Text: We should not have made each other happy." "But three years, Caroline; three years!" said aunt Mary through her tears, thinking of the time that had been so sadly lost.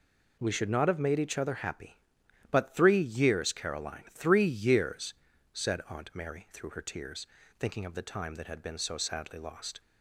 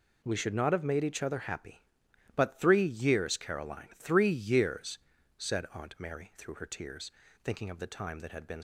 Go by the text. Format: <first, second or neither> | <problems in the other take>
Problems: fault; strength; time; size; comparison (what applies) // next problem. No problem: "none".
first | stops before "so sadly lost"; at 8.5 s